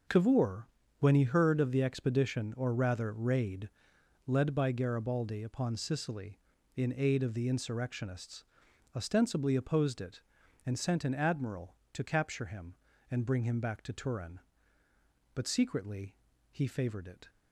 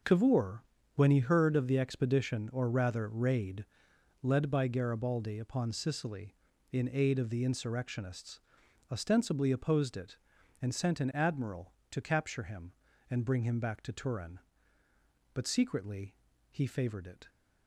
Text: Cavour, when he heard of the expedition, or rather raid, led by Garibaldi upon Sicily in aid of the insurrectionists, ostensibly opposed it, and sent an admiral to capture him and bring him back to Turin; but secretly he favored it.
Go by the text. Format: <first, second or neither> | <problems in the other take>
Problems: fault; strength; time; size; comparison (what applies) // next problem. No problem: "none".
neither | pauses between "secretly" and "he"; the same in both